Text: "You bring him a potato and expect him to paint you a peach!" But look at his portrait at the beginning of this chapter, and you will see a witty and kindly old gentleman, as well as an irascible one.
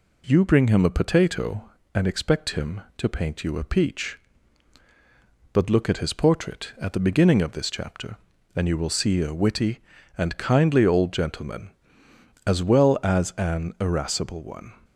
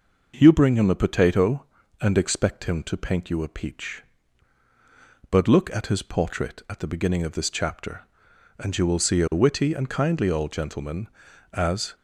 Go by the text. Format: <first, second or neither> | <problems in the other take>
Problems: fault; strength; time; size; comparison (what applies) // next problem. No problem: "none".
first | stops before "well as an irascible one"; at 11.9 s